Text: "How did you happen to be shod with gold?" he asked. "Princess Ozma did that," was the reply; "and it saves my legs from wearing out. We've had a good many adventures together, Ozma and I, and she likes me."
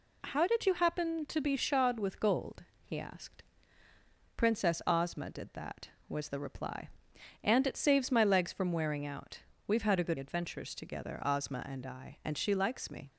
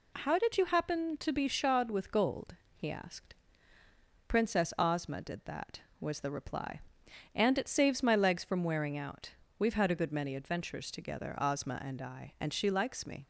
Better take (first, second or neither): second